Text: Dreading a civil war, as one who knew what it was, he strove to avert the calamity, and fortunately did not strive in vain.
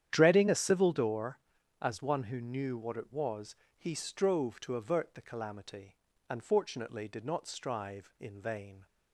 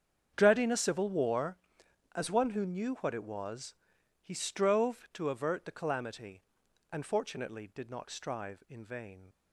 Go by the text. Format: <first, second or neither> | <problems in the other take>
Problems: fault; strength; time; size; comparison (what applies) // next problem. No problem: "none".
second | starts louder than the rest; strong; until 1.1 s; 10 dB; strong in the second // says "door" for "war"; at 0.9 s